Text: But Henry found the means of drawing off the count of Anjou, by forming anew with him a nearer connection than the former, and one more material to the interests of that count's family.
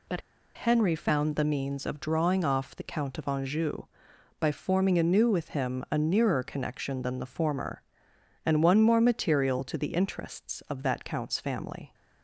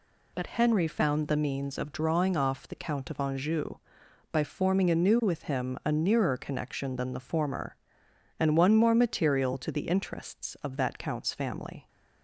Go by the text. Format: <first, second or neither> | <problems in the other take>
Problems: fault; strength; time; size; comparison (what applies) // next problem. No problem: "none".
second | pauses between "But" and "Henry"; slight; at 0.2 s; 0.34 s long